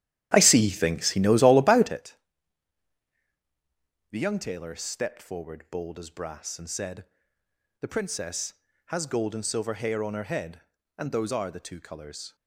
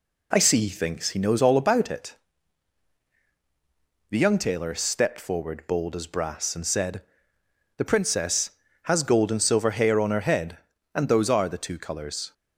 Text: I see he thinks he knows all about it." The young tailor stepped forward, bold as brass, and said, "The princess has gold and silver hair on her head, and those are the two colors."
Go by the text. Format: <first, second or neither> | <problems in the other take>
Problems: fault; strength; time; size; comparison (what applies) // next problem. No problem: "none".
second | starts louder than the rest; strong; until 2.0 s; 11 dB